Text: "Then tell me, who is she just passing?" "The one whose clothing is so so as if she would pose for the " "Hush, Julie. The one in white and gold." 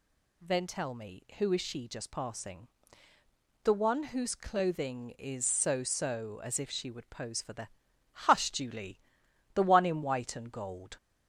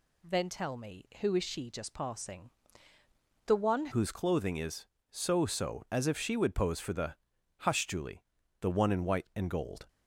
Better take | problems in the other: first | changes voice at "whose"; from 3.9 s on; 5.9 s long

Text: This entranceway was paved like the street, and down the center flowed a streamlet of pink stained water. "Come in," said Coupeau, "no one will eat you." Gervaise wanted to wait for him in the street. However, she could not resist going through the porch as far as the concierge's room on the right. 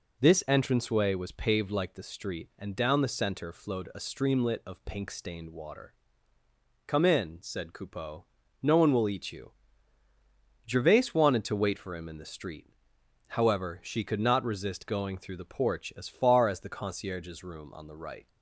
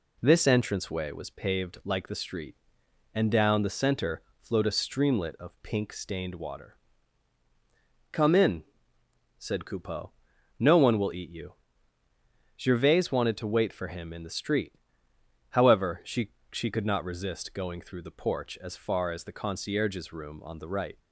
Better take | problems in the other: first | pauses between "center" and "flowed"; slight; at 4.2 s; 0.20 s long // says "she" twice; at 16.5 s

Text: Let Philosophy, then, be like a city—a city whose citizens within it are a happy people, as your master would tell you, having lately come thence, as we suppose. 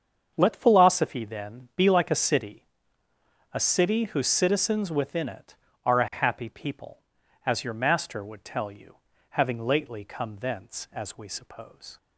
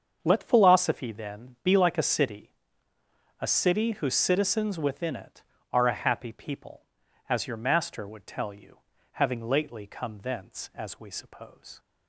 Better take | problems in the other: neither | starts louder than the rest; the same in both

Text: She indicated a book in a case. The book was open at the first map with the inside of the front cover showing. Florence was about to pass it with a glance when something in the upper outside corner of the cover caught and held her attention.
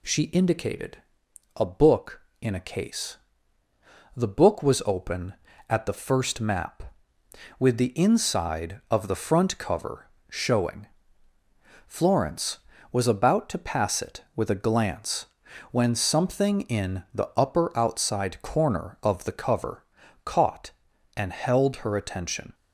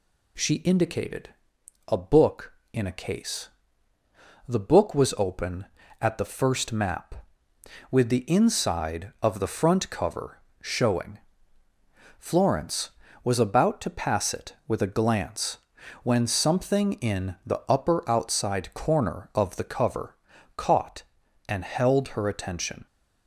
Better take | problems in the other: neither | pauses between "indicated" and "a"; noticeable; the same in both // pauses between "cover" and "showing"; slight; the same in both // pauses between "glance" and "when"; noticeable; the same in both // pauses between "cover" and "caught"; the same in both

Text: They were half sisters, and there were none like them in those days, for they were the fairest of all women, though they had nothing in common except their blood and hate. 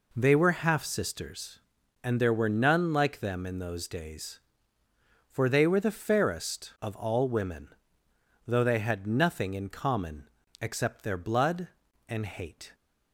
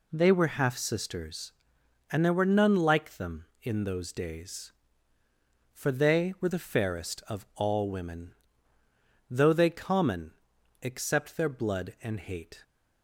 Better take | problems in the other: first | skips "had nothing in"; at 9.6 s // pauses between "common" and "except"; noticeable; at 10.3 s; 0.50 s long; slight in the first

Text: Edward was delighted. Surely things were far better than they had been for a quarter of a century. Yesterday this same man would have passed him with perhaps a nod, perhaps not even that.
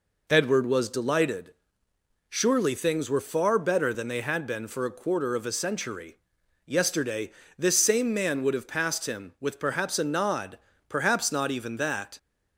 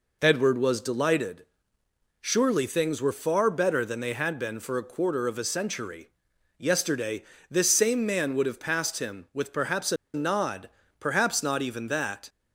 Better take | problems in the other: first | pauses between "Yesterday" and "this"; slight; at 7.2 s; 0.26 s long; slight in the first // pauses between "a" and "nod"; slight; at 9.9 s; 0.18 s long

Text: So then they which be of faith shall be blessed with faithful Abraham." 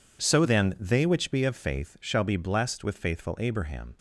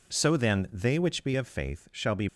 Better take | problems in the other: first | stops before "blessed with faithful Abraham"; at 2.2 s

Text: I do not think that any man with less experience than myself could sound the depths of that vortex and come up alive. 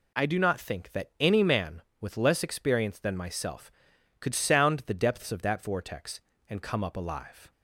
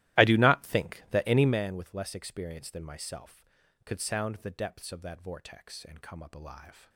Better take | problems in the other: first | starts louder than the rest; strong; until 1.6 s; 15.5 dB

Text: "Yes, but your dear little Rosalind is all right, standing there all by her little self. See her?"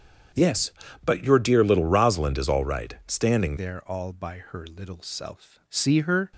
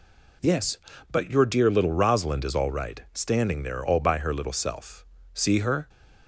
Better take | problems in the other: second | starts louder than the rest; strong; until 1.6 s; 7.5 dB // changes voice at "there"; from 3.5 s on; 2.8 s long

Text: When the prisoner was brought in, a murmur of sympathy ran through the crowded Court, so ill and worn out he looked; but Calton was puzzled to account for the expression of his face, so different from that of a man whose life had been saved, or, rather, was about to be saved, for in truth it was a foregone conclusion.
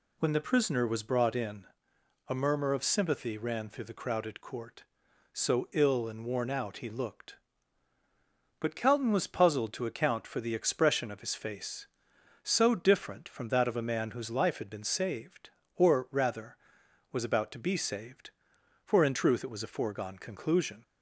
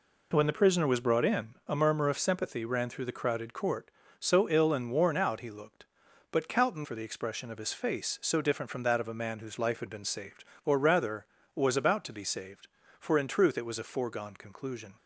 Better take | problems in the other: first | skips "was puzzled to account"; at 6.8 s

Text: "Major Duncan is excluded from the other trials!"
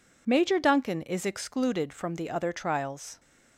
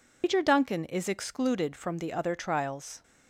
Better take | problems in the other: first | loses the start of "Major"; at 0.2 s; 145 ms

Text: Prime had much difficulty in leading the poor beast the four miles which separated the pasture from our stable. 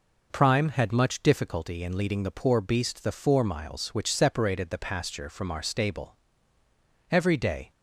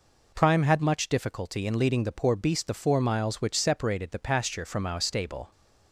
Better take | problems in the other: second | goes on to say "Every day"; from 7.1 s on; 0.60 s long

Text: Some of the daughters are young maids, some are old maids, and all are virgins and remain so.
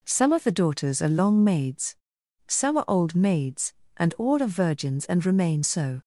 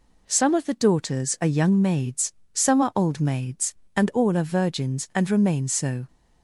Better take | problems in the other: second | says "long" for "young"; at 1.0 s

